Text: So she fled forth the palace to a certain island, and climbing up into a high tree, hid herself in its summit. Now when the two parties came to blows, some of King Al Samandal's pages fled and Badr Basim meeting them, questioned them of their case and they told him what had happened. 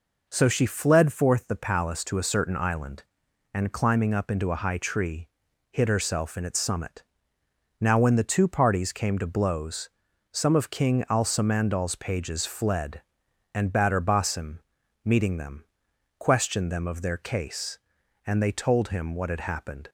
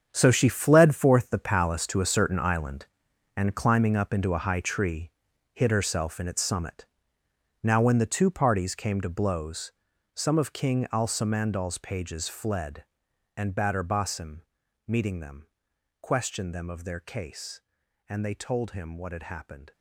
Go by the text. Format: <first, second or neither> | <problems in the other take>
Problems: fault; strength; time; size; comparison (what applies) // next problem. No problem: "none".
first | gets quieter; strong; throughout; 12.5 dB // pauses between "Basim" and "meeting"; noticeable; at 14.4 s; 0.46 s long; noticeable in the first